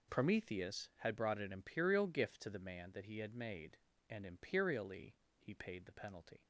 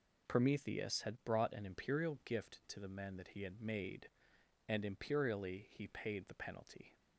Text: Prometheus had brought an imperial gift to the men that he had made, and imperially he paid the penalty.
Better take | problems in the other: second | says "man" for "men"; at 2.5 s // pauses between "imperially" and "he"; slight; at 5.1 s; 0.26 s long

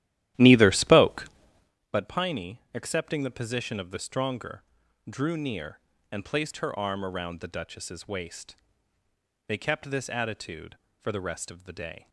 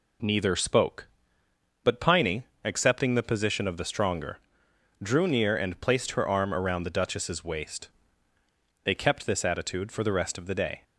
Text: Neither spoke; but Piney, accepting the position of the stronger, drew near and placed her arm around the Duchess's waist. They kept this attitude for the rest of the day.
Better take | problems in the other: second | starts louder than the rest; strong; until 1.8 s; 13 dB

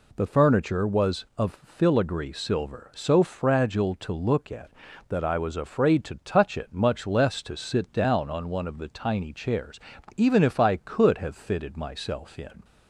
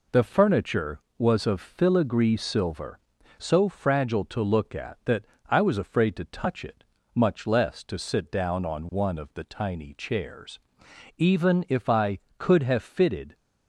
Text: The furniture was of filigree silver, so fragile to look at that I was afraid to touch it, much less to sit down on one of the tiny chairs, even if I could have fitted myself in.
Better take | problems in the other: first | pauses between "that" and "I"; slight; at 5.2 s; 0.24 s long // stops before "myself in"; at 13.3 s

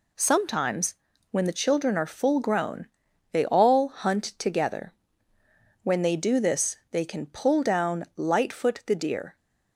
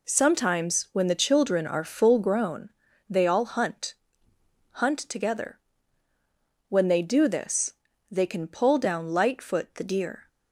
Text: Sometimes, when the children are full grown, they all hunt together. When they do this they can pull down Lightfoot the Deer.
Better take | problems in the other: first | says "hunt" twice; at 4.7 s // pauses between "this" and "they"; at 7.7 s; 0.40 s long; slight in the first

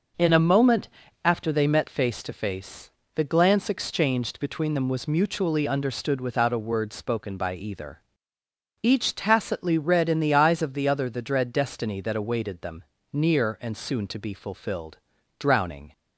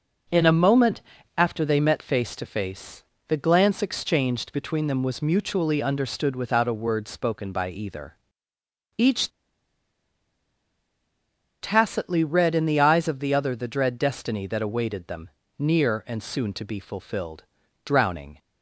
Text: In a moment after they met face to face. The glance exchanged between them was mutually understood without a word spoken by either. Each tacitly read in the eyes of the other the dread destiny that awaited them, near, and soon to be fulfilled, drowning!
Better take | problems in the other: first | pauses between "moment" and "after"; slight; at 1.0 s; 0.36 s long; slight in the first // pauses between "Each" and "tacitly"; strong; at 9.2 s; 2.3 s long

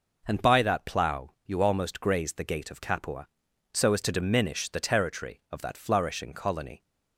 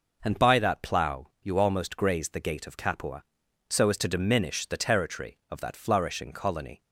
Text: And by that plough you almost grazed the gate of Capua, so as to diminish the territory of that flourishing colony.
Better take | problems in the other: neither | none

